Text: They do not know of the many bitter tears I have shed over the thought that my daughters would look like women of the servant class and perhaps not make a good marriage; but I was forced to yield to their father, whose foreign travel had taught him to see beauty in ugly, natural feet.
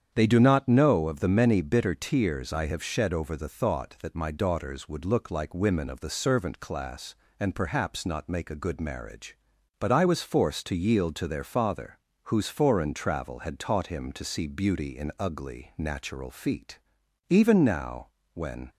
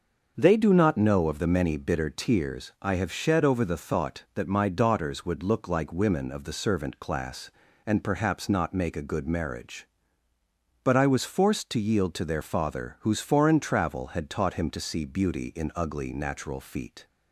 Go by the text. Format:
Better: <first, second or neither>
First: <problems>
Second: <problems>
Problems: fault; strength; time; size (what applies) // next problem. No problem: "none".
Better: second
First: starts louder than the rest; strong; until 1.1 s; 8 dB // goes on to say "Even now when"; from 17.2 s on; 1.4 s long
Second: starts louder than the rest; until 1.3 s; 6.5 dB